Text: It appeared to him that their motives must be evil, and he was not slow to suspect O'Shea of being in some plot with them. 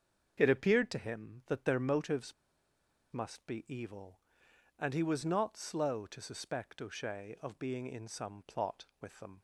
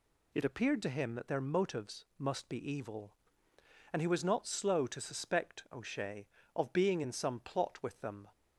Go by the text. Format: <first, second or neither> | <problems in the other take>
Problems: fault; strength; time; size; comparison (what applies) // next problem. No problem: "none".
second | starts louder than the rest; until 1.4 s; 7 dB // pauses between "motives" and "must"; noticeable; at 2.3 s; 0.80 s long